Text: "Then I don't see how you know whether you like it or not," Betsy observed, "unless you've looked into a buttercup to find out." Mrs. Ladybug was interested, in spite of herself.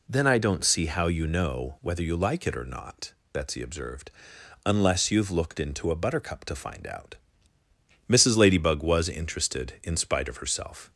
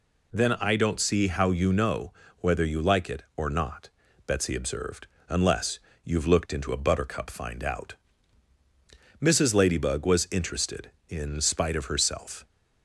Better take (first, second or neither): first